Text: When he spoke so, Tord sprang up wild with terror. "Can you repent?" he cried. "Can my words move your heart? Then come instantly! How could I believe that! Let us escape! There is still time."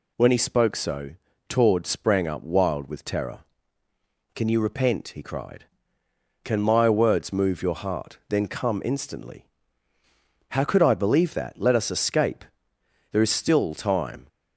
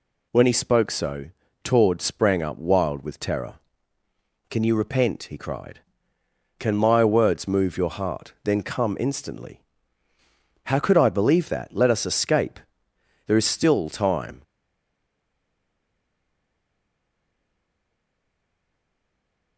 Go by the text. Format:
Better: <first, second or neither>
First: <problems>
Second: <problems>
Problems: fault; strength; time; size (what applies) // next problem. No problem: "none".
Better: first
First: none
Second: stays silent after the last word; strong; from 14.4 s on; 5.1 s long